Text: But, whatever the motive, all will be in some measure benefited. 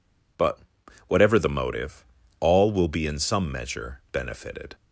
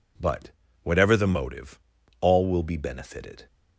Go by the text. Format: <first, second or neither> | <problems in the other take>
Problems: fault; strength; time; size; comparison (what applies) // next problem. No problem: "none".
first | skips "in some measure"; at 2.7 s